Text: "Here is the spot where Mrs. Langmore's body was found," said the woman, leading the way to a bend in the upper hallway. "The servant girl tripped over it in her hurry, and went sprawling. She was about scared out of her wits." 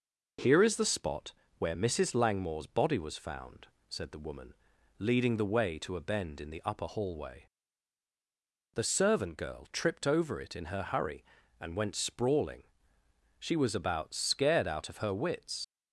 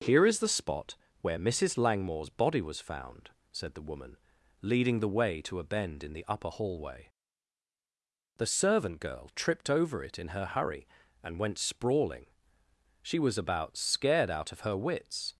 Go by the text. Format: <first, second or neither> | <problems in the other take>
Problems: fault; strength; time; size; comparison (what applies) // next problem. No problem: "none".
second | pauses between "spot" and "where"; slight; at 1.3 s; 0.24 s long; slight in the second // leaves "wits" unfinished; at 15.6 s; 90 ms